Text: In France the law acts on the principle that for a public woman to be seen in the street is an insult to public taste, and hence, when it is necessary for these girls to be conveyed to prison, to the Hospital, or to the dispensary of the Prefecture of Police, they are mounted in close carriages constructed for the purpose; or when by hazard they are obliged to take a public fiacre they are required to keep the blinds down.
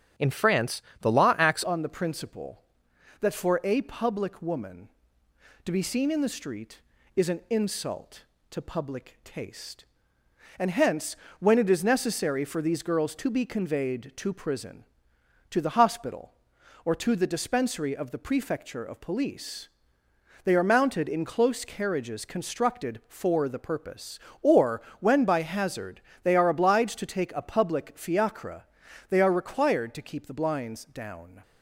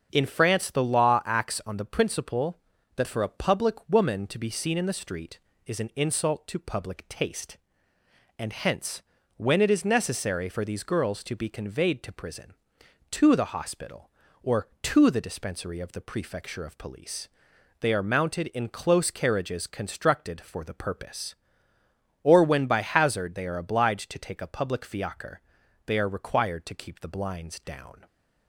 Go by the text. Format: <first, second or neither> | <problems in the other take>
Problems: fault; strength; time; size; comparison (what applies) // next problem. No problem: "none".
second | starts louder than the rest; strong; until 1.4 s; 8.5 dB; also in the second // pauses between "France" and "the"; slight; at 0.8 s; 0.20 s long // changes voice at "on"; from 1.6 s on; 29.8 s long // pauses between "or" and "when"; slight; at 24.8 s; 0.18 s long // pauses between "hazard" and "they"; slight; at 26.0 s; 0.22 s long // pauses between "fiacre" and "they"; noticeable; at 28.6 s; 0.46 s long; also in the second